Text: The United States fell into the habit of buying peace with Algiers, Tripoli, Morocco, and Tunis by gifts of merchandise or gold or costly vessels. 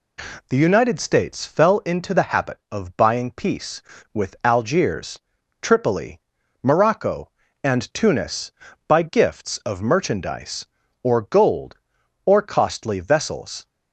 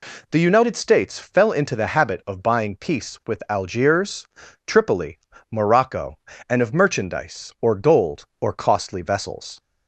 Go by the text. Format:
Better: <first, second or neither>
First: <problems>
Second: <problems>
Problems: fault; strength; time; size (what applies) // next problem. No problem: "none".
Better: first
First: none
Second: skips "Tunis by gifts"; at 6.6 s